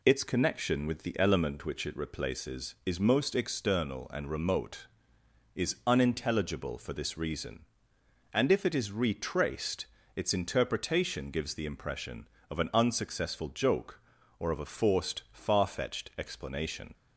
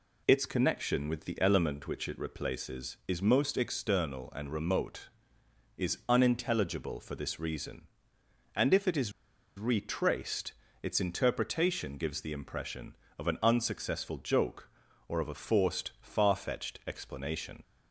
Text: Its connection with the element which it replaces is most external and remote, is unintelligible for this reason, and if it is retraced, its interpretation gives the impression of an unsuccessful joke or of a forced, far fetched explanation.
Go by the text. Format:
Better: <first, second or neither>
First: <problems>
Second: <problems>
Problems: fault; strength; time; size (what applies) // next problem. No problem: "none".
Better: first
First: none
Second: pauses between "is" and "retraced"; noticeable; at 9.1 s; 0.46 s long